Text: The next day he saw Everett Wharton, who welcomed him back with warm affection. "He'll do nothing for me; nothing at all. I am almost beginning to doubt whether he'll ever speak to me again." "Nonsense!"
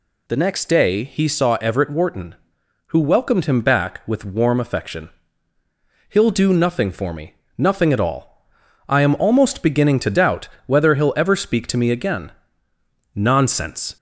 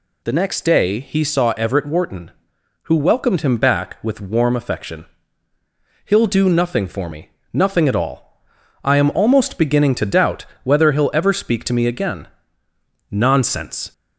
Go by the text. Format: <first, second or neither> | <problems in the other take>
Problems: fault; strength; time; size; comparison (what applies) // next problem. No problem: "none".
neither | pauses between "doubt" and "whether"; slight; the same in both